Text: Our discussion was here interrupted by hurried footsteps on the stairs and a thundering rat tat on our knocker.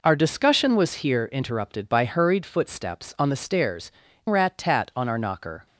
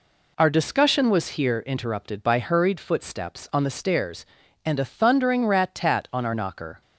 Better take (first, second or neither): second